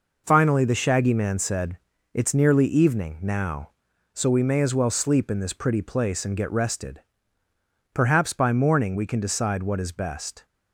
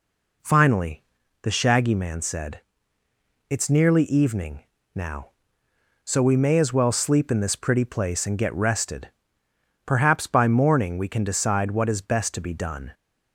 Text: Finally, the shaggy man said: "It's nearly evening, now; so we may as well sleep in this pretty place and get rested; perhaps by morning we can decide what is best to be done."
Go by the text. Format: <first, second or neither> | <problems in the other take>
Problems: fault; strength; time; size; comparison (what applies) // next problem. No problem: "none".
second | stops before "to be done"; at 10.4 s